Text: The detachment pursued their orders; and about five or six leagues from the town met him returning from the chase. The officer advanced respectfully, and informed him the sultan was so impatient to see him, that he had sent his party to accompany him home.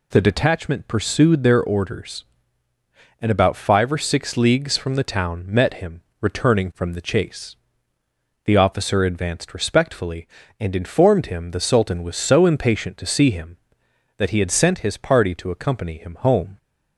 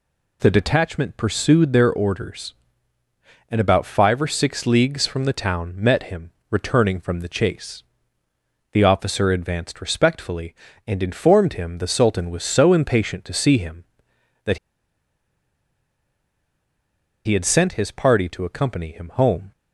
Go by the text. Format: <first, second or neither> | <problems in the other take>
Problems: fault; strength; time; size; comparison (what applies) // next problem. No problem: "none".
first | pauses between "him" and "returning"; slight; at 6.3 s; 0.18 s long; slight in the first // pauses between "that" and "he"; strong; at 14.5 s; 2.6 s long